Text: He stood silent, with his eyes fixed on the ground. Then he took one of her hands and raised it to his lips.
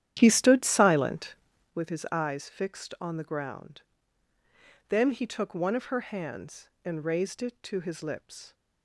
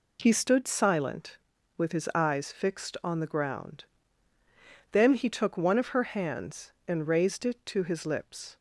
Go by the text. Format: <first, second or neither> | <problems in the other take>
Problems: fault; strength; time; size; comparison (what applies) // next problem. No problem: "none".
second | starts louder than the rest; strong; until 1.7 s; 10.5 dB